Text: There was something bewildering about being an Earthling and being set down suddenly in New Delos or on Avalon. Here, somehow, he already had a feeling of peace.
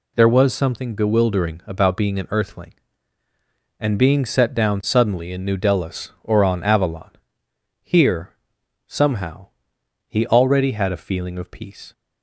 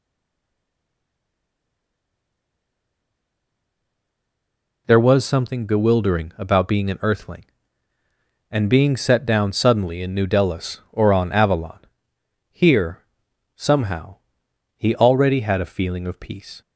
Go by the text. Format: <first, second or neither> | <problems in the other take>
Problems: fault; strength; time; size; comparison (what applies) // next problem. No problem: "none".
first | stays silent before the first word; strong; until 4.8 s; 4.8 s long